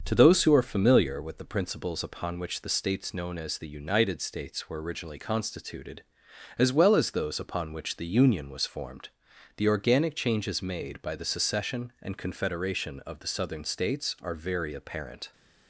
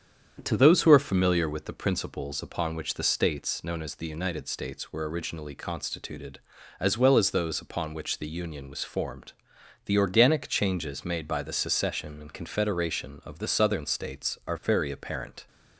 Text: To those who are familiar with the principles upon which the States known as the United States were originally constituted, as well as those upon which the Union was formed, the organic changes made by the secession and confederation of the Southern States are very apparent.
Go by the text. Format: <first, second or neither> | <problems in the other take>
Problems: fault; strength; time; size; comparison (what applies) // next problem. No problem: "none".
neither | starts louder than the rest; the same in both